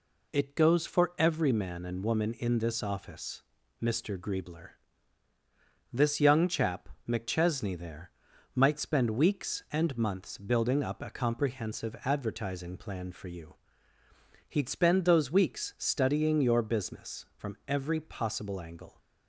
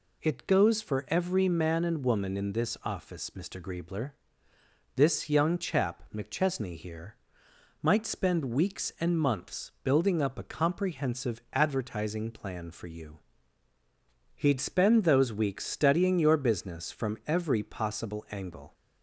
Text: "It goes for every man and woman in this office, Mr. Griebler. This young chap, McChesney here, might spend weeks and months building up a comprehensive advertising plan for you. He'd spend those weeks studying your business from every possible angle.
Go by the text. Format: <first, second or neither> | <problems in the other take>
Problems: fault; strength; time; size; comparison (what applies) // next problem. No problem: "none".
second | says "there" for "here"; at 7.7 s